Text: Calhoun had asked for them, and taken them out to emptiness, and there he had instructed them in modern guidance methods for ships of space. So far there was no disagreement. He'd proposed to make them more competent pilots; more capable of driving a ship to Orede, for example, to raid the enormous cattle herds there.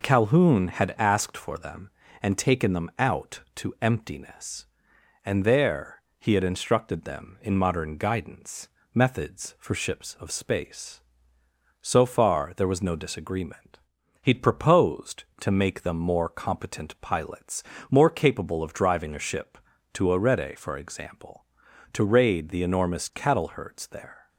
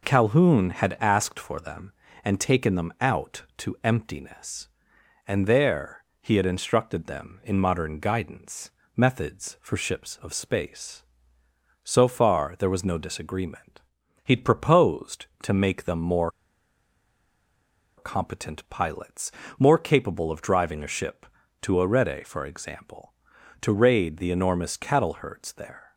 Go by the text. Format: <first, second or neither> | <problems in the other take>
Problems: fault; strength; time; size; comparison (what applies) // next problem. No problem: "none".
first | pauses between "there" and "he"; slight; at 6.0 s; 0.16 s long; slight in the first // pauses between "guidance" and "methods"; slight; at 8.6 s; 0.26 s long; slight in the first // pauses between "more" and "competent"; strong; at 16.2 s; 1.6 s long